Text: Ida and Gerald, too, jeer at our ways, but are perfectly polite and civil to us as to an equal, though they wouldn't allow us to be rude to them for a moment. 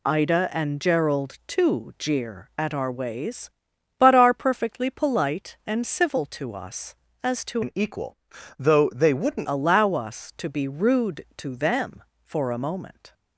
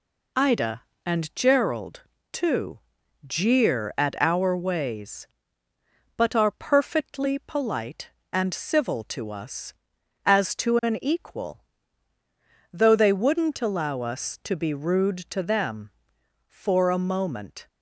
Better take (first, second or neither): second